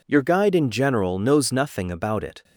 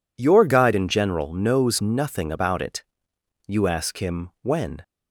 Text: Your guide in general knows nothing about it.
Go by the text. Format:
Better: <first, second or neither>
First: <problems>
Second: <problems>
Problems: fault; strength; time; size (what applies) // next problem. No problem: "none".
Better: first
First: none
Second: goes on to say "You ask him when"; from 3.4 s on; 1.3 s long